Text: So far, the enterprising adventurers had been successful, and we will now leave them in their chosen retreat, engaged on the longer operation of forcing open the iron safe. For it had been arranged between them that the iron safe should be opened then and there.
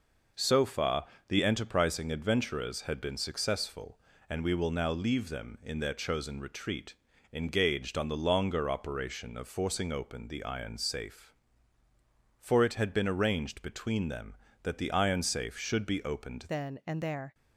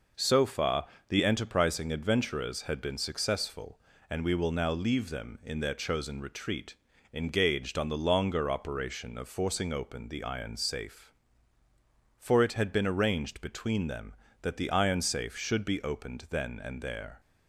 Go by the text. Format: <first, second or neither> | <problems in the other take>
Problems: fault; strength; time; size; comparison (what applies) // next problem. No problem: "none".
second | changes voice at "then"; from 16.4 s on; 0.9 s long